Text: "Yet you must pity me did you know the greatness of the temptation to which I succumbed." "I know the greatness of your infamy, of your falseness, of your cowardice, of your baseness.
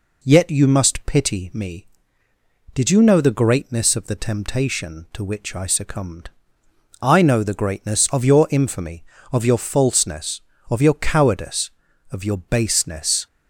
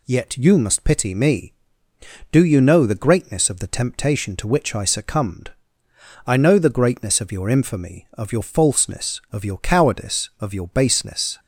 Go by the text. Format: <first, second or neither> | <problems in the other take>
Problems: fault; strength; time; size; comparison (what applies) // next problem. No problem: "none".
first | says "do" for "did"; at 2.3 s